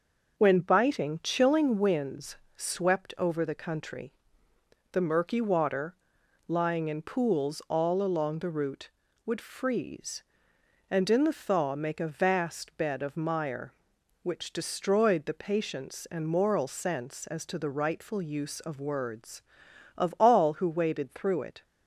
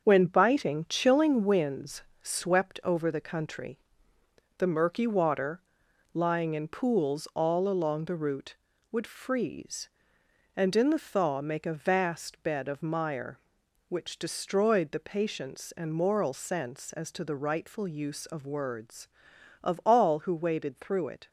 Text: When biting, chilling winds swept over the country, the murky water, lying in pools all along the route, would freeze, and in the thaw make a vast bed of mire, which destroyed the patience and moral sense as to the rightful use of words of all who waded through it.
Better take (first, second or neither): first